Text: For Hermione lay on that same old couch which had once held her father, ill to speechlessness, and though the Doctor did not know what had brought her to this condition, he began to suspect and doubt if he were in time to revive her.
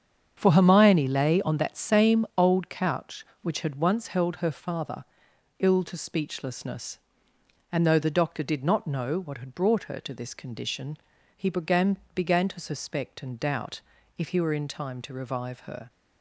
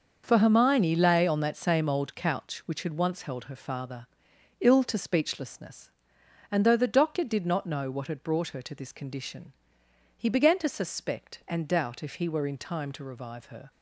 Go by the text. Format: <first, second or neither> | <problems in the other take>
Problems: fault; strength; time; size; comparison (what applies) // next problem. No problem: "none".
second | starts louder than the rest; strong; until 1.3 s; 7.5 dB; also in the second // says "began" twice; at 12.1 s // pauses between "doubt" and "if"; at 13.8 s; 0.38 s long